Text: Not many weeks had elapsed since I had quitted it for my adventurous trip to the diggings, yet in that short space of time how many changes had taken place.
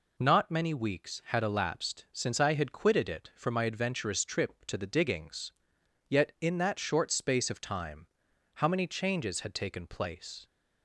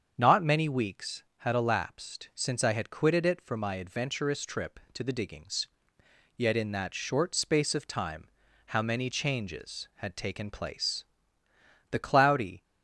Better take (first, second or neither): first